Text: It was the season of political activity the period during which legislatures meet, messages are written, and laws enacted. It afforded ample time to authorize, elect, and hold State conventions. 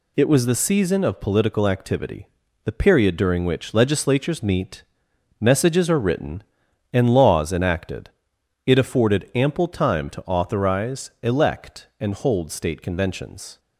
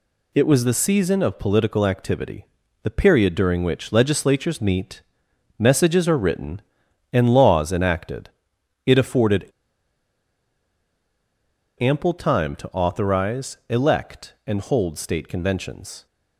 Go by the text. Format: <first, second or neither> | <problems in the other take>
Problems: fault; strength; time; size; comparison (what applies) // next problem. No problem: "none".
first | pauses between "activity" and "the"; slight; at 2.4 s; 0.36 s long; slight in the first // pauses between "afforded" and "ample"; strong; at 9.4 s; 2.3 s long